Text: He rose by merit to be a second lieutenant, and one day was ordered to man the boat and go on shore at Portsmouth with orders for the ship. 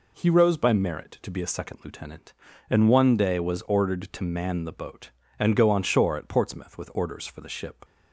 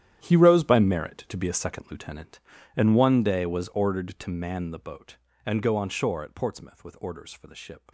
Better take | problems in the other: first | gets quieter; strong; throughout; 15.5 dB

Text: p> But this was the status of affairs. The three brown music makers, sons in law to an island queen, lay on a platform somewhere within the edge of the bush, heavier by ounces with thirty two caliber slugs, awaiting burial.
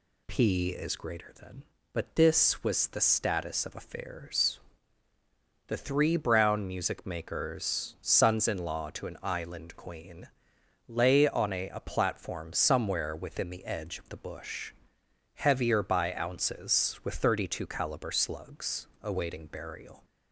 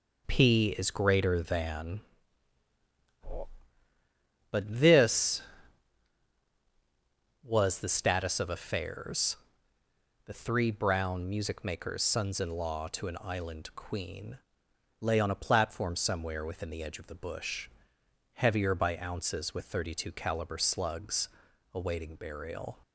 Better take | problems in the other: second | says "a" twice; at 11.6 s

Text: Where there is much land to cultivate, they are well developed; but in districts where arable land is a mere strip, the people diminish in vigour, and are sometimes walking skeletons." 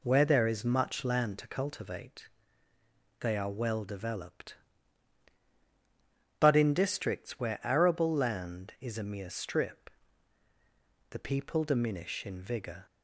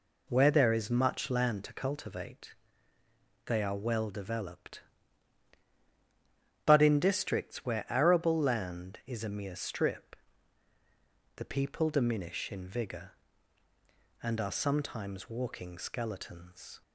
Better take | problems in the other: second | stops before "and are sometimes walking skeletons"; at 12.8 s

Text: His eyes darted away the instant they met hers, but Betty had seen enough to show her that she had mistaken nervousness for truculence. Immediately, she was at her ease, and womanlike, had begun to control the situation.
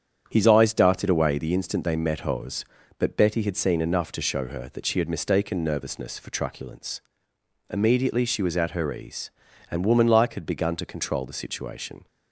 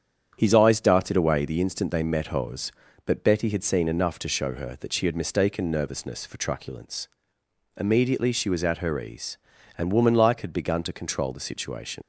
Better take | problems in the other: first | starts louder than the rest; strong; until 1.3 s; 8 dB; strong in the first // leaves "situation" unfinished; at 12.0 s; 115 ms

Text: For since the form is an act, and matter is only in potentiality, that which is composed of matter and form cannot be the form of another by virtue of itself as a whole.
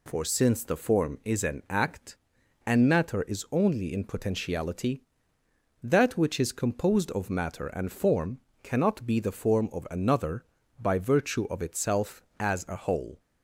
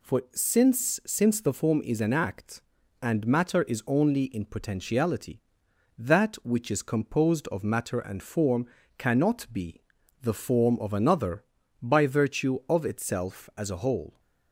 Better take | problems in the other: first | says "since" twice; at 1.0 s // pauses between "form" and "cannot"; slight; at 8.6 s; 0.32 s long; slight in the first // pauses between "be" and "the"; at 9.8 s; 0.38 s long

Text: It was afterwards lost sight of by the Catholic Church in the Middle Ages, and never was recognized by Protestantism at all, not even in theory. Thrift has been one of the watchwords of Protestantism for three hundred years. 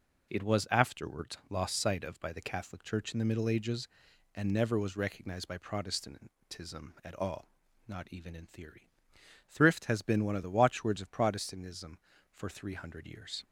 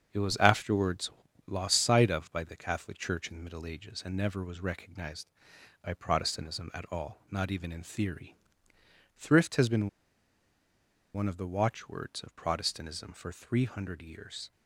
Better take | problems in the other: first | starts louder than the rest; strong; until 1.5 s; 7 dB // pauses between "afterwards" and "lost"; slight; at 1.1 s; 0.36 s long // pauses between "been" and "one"; strong; at 9.8 s; 1.2 s long

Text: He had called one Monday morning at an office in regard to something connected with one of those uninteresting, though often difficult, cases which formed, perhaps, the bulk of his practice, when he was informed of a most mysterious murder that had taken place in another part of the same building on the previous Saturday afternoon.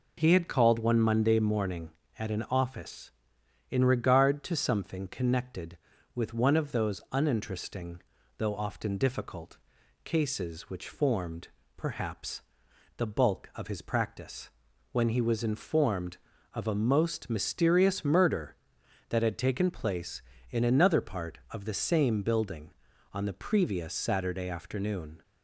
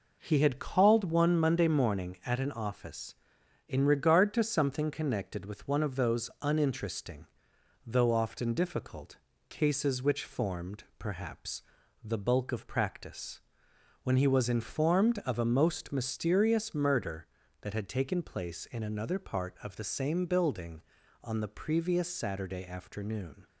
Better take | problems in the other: first | skips "his"; at 12.6 s

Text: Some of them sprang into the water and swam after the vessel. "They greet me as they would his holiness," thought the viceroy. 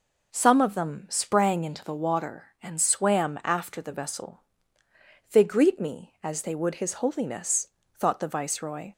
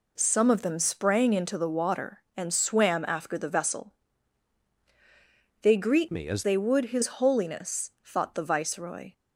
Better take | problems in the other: first | changes voice from "me" to "as"; from 6.1 to 6.4 s; 0.3 s long

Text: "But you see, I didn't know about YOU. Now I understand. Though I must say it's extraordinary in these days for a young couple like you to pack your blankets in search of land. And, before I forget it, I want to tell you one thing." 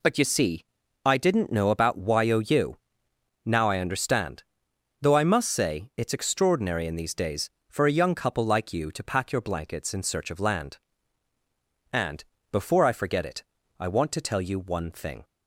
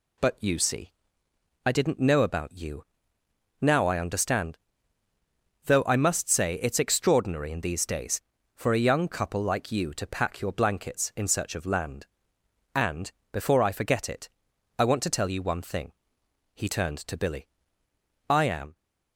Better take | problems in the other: first | goes on to say "He turned to Billy I am"; strong; from 16.5 s on; 2.2 s long

